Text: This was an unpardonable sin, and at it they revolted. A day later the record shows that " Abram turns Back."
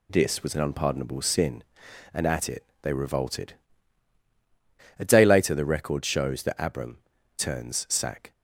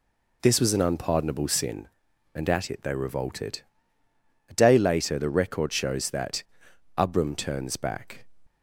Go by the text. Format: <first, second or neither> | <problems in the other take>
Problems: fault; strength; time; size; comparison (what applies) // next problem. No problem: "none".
second | pauses between "it" and "they"; slight; at 2.6 s; 0.18 s long // pauses between "Abram" and "turns"; at 6.9 s; 0.40 s long // says "Sack" for "Back"; at 7.8 s